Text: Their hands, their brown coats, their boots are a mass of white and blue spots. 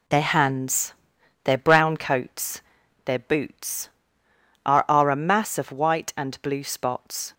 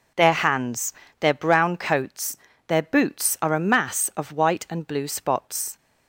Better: second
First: says "are" twice; at 4.8 s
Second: none

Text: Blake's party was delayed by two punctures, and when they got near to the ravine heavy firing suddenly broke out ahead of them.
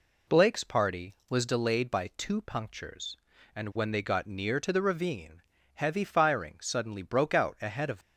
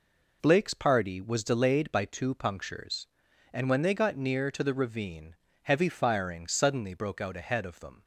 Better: second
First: pauses between "ravine" and "heavy"; slight; at 5.4 s; 0.32 s long // stops before "them"; at 8.0 s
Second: pauses between "ravine" and "heavy"; slight; at 5.3 s; 0.28 s long

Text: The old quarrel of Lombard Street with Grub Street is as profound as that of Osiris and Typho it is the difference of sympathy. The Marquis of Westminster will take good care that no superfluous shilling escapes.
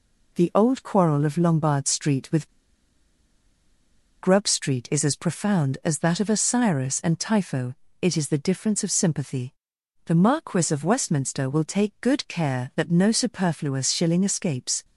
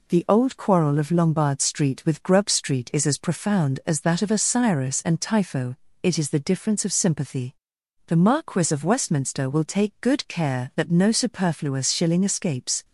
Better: second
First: pauses between "with" and "Grub"; strong; at 2.4 s; 1.7 s long // pauses between "Typho" and "it"; slight; at 7.7 s; 0.28 s long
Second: pauses between "Typho" and "it"; slight; at 5.7 s; 0.28 s long

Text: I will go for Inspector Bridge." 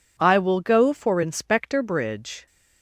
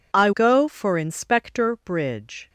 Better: first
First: none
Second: skips "will"; at 0.3 s

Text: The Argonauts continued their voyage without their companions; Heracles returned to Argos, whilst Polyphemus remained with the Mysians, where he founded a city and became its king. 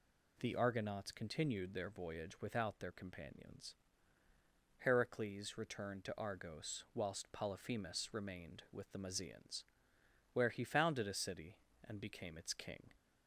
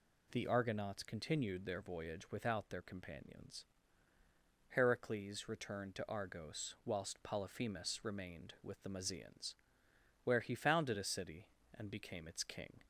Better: neither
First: none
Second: none

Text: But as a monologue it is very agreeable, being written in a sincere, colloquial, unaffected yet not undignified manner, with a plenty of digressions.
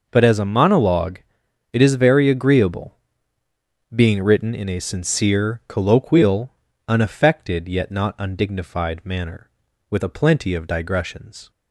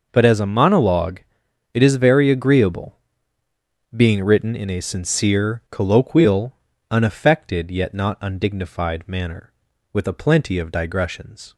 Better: neither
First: pauses between "monologue" and "it"; noticeable; at 1.2 s; 0.50 s long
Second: pauses between "monologue" and "it"; noticeable; at 1.2 s; 0.50 s long

